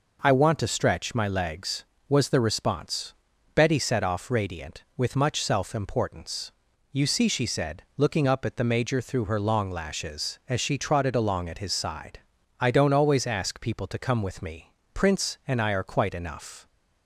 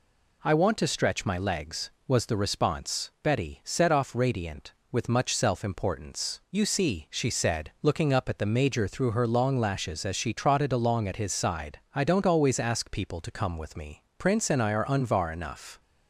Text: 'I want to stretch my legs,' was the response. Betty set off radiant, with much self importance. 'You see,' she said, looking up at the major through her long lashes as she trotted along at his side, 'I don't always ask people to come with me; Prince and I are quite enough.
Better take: first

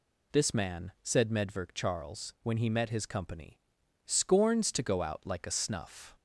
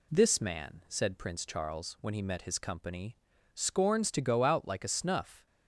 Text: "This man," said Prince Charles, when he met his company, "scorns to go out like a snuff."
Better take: second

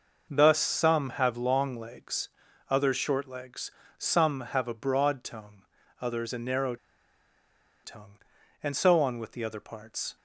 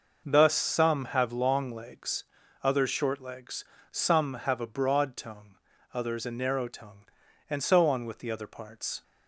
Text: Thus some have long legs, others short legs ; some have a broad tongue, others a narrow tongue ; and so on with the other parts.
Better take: second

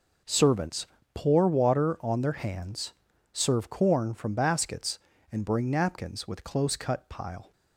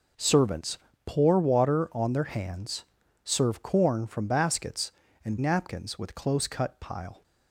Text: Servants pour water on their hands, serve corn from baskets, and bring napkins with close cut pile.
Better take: first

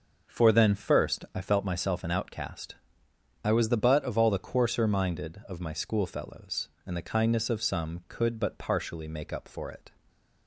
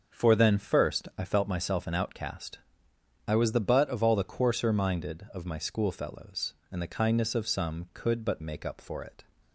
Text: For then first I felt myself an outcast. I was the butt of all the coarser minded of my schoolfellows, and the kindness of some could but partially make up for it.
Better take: first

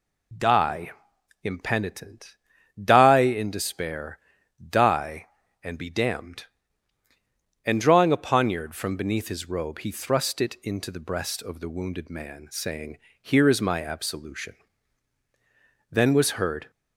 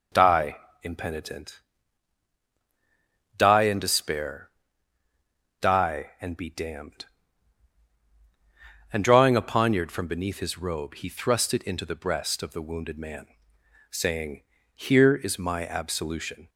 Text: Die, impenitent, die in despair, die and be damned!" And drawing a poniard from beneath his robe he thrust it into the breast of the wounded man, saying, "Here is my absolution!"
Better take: second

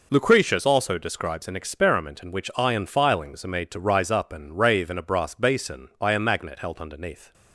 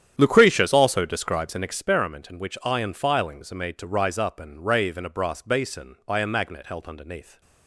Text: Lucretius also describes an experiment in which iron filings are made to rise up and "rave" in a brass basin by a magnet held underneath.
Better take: first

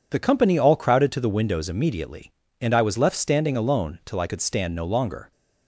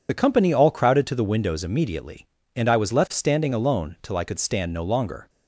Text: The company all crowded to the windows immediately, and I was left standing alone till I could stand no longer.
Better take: first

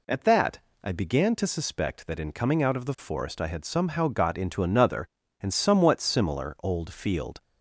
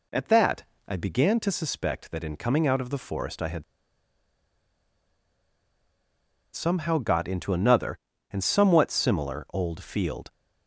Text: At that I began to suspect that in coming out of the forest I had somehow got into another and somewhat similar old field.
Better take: first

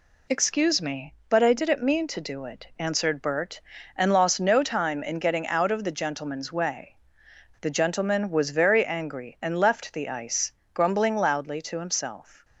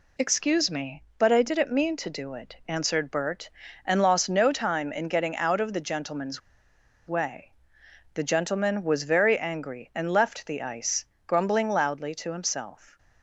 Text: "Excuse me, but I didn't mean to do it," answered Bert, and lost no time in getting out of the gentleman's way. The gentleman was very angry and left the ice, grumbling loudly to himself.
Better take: first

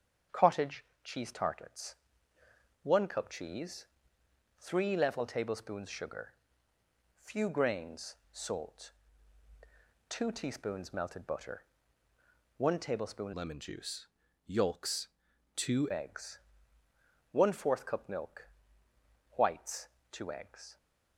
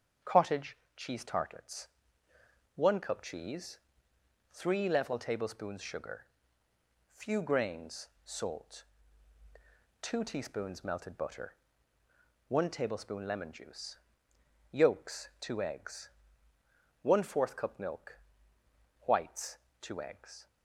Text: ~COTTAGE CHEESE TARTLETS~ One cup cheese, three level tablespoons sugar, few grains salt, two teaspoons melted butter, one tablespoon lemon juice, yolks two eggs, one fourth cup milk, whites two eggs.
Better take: second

